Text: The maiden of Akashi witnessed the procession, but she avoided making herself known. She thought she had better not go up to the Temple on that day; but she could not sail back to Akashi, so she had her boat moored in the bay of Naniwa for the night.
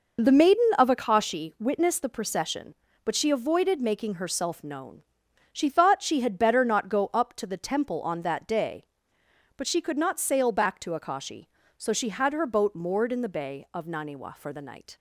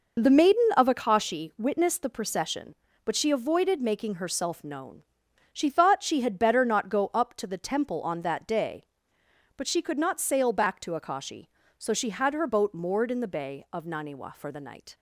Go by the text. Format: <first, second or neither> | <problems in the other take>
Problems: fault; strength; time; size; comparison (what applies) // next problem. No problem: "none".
neither | none